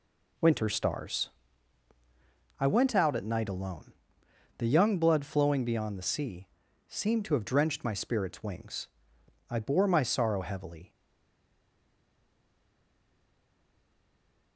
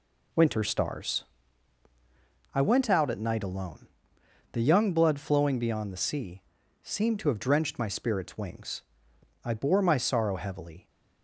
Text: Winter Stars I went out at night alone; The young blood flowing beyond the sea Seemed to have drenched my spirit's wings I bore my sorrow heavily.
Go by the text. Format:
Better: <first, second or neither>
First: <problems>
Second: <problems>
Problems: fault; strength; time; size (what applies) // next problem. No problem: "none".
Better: second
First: pauses between "Stars" and "I"; strong; at 1.3 s; 1.3 s long // pauses between "sea" and "Seemed"; at 6.4 s; 0.42 s long // pauses between "wings" and "I"; noticeable; at 8.8 s; 0.62 s long // stays silent after the last word; strong; from 10.9 s on; 3.6 s long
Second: pauses between "Stars" and "I"; strong; at 1.2 s; 1.3 s long // pauses between "sea" and "Seemed"; at 6.4 s; 0.42 s long // pauses between "wings" and "I"; noticeable; at 8.8 s; 0.62 s long